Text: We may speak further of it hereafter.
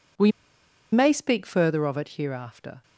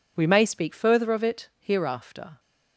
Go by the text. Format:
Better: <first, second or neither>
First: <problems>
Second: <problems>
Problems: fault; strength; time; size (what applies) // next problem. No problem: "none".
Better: second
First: pauses between "We" and "may"; noticeable; at 0.3 s; 0.61 s long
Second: none